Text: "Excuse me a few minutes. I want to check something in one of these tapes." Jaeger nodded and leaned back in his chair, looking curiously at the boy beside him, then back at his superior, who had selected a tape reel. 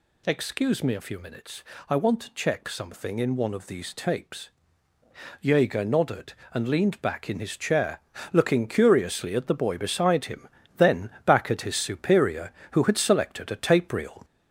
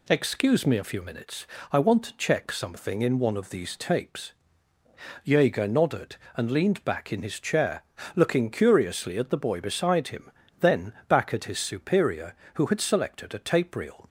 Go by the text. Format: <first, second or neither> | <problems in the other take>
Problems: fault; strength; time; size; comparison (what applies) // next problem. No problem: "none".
second | gets louder; noticeable; throughout; 4 dB // pauses between "then" and "back"; slight; at 11.1 s; 0.16 s long; slight in the second